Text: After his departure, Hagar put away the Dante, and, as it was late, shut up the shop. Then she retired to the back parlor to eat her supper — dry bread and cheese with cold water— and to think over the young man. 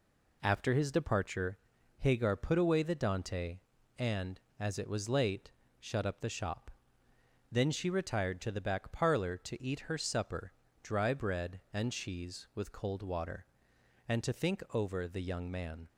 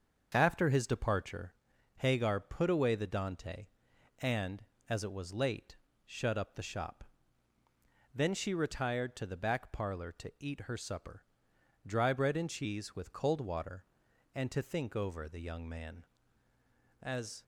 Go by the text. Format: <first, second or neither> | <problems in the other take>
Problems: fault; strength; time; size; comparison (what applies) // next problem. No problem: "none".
first | starts louder than the rest; until 1.3 s; 6.5 dB // goes on to say "As"; slight; from 17.0 s on; 0.42 s long